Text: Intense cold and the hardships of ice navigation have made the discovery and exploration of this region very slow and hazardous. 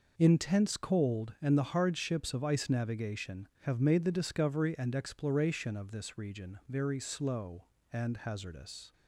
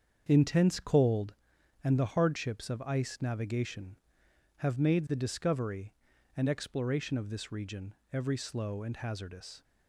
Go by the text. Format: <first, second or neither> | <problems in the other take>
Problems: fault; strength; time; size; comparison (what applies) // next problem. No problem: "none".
first | starts louder than the rest; strong; until 1.3 s; 7 dB // says "every" for "very"; at 8.1 s